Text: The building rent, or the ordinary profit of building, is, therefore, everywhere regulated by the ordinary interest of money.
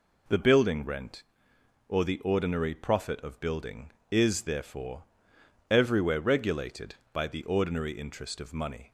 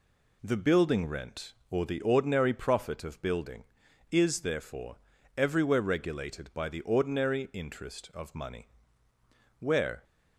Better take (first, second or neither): first